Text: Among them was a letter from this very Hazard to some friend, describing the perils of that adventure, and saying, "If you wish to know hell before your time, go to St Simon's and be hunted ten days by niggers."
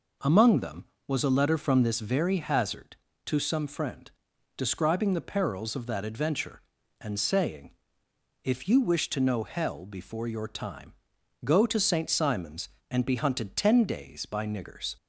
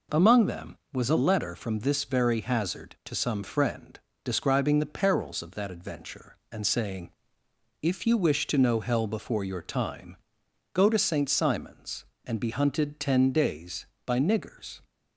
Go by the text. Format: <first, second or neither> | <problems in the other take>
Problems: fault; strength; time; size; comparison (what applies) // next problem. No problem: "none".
neither | none